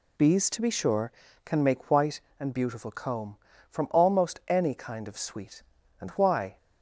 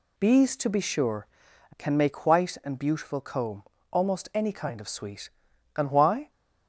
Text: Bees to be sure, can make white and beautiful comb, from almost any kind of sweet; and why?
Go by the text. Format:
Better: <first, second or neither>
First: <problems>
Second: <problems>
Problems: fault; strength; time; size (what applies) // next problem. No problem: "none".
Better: first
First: none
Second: skips "from"; at 3.7 s